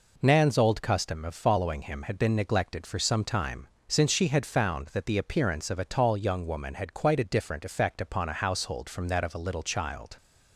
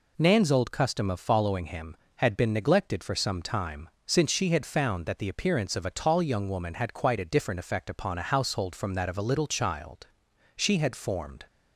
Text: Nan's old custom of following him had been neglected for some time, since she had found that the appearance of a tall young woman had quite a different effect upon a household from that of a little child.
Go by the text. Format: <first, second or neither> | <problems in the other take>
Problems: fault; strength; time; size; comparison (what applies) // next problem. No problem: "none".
first | goes on to say "She had formed"; noticeable; from 10.5 s on; 0.90 s long